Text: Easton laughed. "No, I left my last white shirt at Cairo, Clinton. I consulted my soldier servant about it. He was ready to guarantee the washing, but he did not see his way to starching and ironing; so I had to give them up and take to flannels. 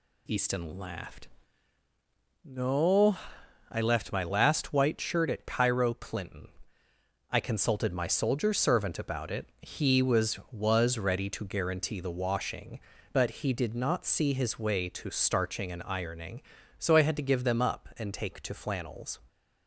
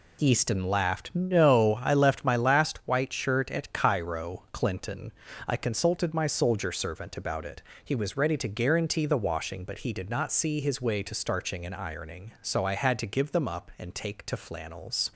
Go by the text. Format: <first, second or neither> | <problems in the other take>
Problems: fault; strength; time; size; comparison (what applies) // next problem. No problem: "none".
second | says "was" twice; at 10.5 s